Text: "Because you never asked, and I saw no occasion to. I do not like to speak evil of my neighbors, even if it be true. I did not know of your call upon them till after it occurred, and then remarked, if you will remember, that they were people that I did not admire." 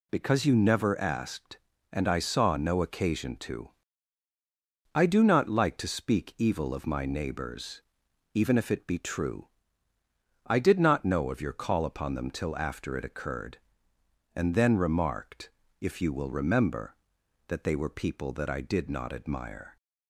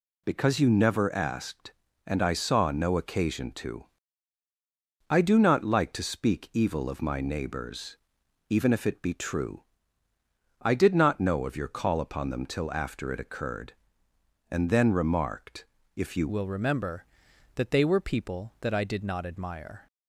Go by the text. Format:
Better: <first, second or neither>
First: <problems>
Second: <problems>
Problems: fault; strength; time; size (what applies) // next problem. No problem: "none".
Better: first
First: none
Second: changes voice at "will"; from 16.2 s on; 3.6 s long